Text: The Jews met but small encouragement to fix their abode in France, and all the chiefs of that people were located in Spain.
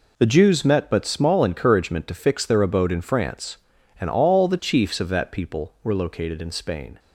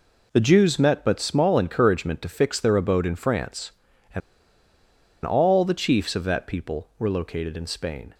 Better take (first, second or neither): first